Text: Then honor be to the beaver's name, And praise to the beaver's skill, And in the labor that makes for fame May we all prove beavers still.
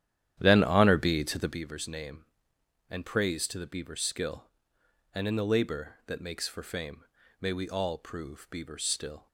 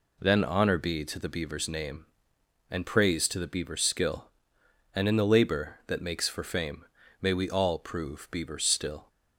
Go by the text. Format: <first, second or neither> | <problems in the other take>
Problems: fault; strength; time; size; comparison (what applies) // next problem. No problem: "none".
second | starts louder than the rest; strong; until 1.6 s; 11 dB // pauses between "fame" and "May"; at 7.0 s; 0.38 s long; also in the second